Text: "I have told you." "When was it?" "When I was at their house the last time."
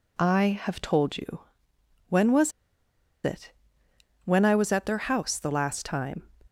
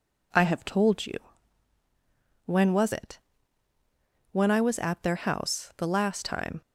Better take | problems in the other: second | pauses between "was" and "it"; noticeable; at 2.5 s; 0.73 s long

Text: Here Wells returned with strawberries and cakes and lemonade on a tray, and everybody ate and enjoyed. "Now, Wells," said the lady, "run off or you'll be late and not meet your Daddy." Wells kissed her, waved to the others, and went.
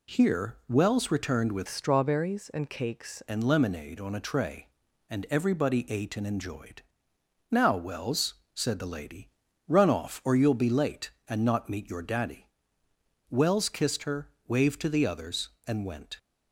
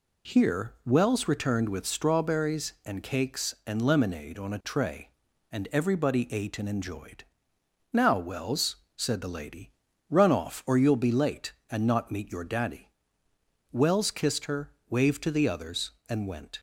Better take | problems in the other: second | changes voice from "strawberries" to "cakes"; from 1.6 to 3.2 s; 1.6 s long

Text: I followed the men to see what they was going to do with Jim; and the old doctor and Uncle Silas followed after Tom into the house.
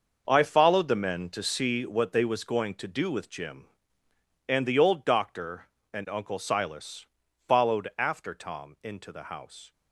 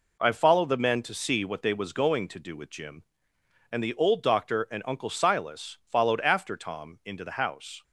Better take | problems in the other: second | gets quieter; strong; throughout; 11.5 dB // pauses between "Silas" and "followed"; at 7.0 s; 0.42 s long

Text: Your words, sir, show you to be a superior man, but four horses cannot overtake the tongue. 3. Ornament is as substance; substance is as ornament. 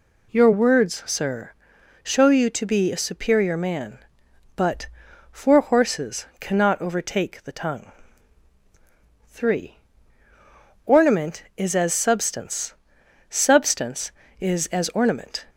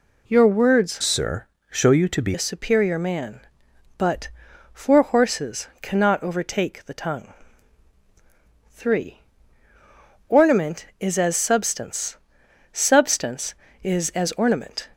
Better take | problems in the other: first | changes voice from "sir" to "be"; from 1.0 to 2.3 s; 1.3 s long // pauses between "but" and "four"; at 4.2 s; 0.44 s long; also in the first // pauses between "horses" and "cannot"; slight; at 5.6 s; 0.16 s long; slight in the first

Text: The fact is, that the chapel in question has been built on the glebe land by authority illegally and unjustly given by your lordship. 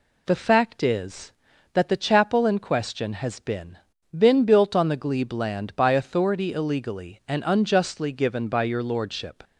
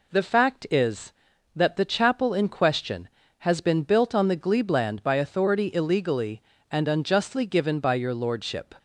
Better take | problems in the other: second | says "been" twice; at 4.1 s

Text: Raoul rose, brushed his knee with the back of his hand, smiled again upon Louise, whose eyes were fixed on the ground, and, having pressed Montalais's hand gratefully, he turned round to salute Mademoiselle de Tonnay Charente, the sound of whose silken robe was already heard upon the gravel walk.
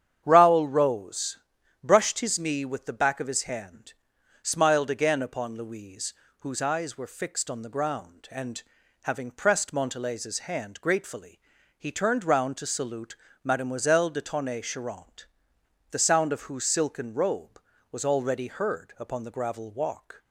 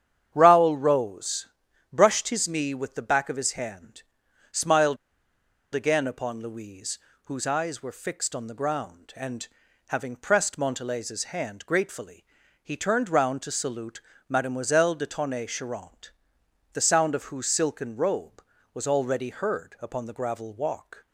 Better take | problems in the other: first | starts louder than the rest; strong; until 1.3 s; 9 dB; strong in the first // pauses between "smiled" and "again"; noticeable; at 4.9 s; 0.77 s long // pauses between "salute" and "Mademoiselle"; slight; at 14.0 s; 0.26 s long; slight in the first

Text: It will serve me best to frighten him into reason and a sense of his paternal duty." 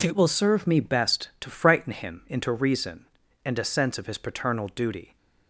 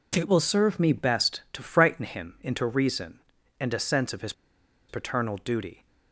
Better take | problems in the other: first | pauses between "his" and "paternal"; noticeable; at 4.3 s; 0.56 s long

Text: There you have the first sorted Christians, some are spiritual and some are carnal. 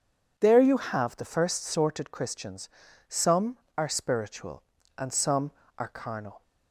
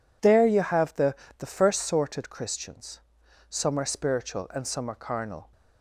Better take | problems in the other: first | says "the" twice; at 1.3 s

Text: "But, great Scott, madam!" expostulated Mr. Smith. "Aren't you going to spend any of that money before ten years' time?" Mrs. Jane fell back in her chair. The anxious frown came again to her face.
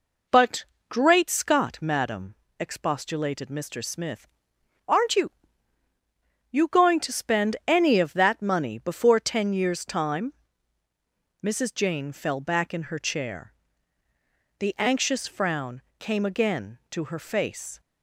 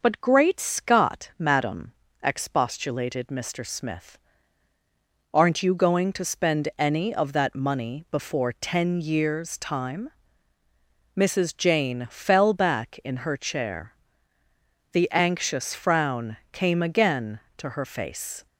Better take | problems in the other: second | says "you" twice; at 6.4 s // pauses between "frown" and "came"; slight; at 15.7 s; 0.18 s long

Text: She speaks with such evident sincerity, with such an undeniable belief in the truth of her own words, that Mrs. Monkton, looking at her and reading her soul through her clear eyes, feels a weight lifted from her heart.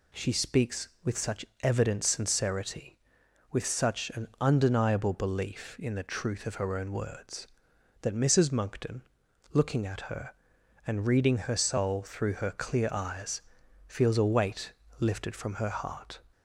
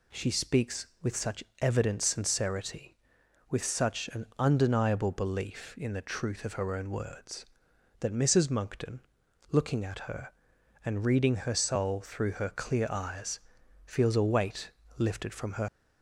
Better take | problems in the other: first | pauses between "such" and "evident"; slight; at 1.4 s; 0.20 s long; slight in the first // pauses between "weight" and "lifted"; slight; at 14.7 s; 0.26 s long; slight in the first // stops before "heart"; at 15.6 s

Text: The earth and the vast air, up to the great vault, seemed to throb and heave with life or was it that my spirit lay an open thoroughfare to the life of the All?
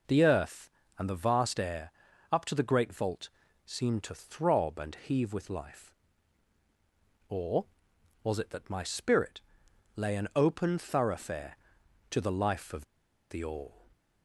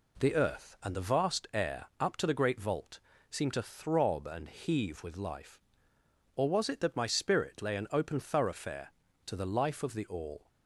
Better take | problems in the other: second | pauses between "spirit" and "lay"; noticeable; at 9.4 s; 0.56 s long // pauses between "of" and "the"; at 12.8 s; 0.45 s long

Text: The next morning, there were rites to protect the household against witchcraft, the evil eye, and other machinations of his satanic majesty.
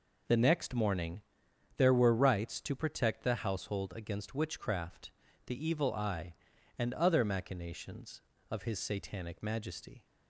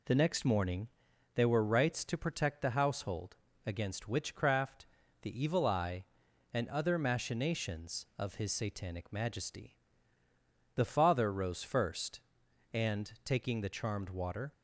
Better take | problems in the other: first | pauses between "household" and "against"; slight; at 3.3 s; 0.32 s long // goes on to say "The father rose first and taking the charmed water"; strong; from 10.7 s on; 3.7 s long

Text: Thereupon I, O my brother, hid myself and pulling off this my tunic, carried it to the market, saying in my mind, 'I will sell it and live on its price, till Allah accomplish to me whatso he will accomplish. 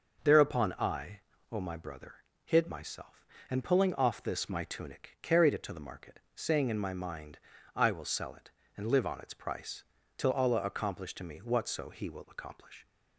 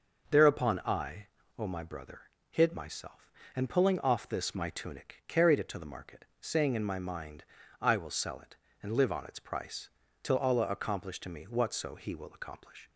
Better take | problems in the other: neither | none

